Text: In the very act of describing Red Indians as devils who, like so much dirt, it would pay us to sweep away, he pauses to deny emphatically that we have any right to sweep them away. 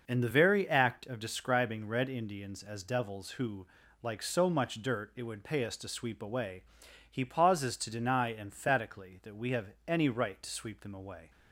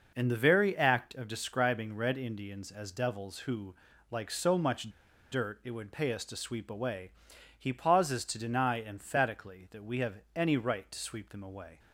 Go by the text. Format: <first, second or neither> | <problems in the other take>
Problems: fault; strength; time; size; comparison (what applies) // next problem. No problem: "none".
first | pauses between "much" and "dirt"; at 4.9 s; 0.40 s long